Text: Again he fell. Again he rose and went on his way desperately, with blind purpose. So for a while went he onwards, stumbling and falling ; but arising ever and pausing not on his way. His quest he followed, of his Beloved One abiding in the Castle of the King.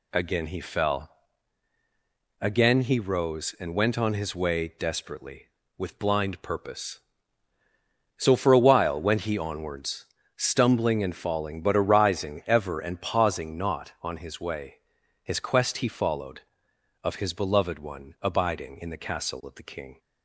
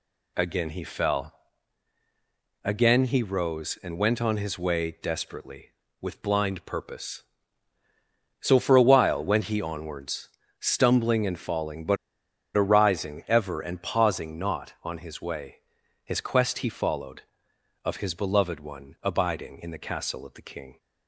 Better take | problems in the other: first | pauses between "but" and "arising"; noticeable; at 11.9 s; 0.60 s long

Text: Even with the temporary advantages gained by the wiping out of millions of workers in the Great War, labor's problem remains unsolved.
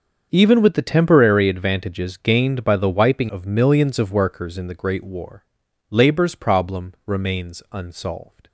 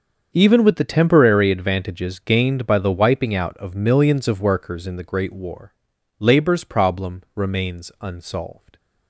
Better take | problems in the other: second | starts louder than the rest; until 1.3 s; 7 dB; also in the second // skips "out"; at 3.2 s

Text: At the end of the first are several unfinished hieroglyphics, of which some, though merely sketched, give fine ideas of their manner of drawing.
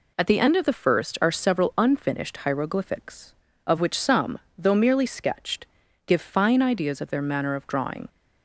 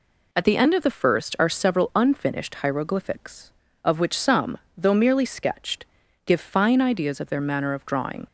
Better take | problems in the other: neither | none

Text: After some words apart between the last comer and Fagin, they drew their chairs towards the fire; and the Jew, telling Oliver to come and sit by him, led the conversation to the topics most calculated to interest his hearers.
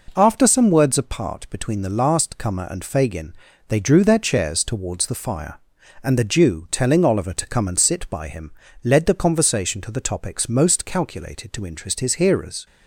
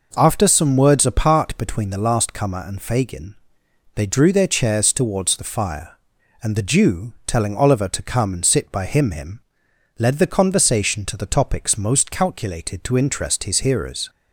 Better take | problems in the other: first | says "him" twice; at 9.1 s

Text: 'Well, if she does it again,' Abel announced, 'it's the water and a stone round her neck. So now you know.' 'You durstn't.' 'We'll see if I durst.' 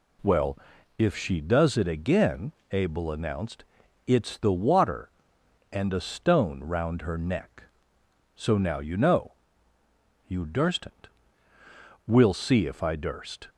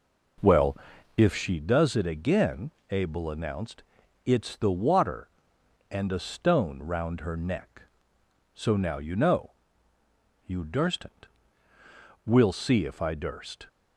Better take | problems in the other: first | starts louder than the rest; noticeable; until 1.5 s; 5 dB

